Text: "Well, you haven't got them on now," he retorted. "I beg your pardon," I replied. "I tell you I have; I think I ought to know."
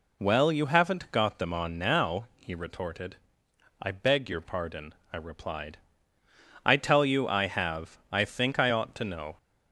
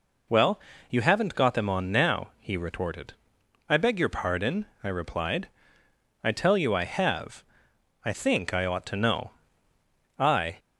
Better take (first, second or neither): first